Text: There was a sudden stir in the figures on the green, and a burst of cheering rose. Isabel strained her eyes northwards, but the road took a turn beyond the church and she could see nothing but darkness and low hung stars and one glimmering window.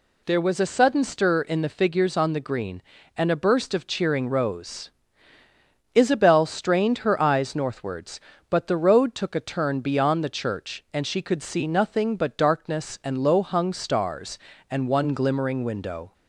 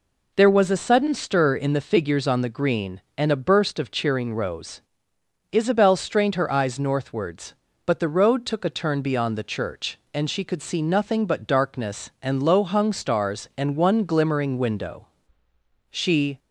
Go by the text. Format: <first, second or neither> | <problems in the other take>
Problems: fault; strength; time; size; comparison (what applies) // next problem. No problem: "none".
first | goes on to say "She"; slight; from 15.9 s on; 0.48 s long